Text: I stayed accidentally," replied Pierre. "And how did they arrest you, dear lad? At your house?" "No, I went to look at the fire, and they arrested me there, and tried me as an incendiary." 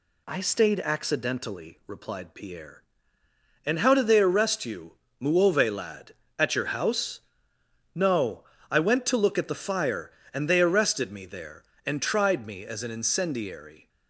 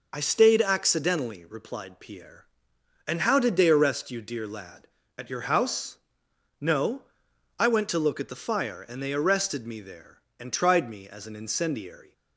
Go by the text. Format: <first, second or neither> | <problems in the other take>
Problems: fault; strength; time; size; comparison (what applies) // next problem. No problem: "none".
second | says "muove" for "dear"; at 5.2 s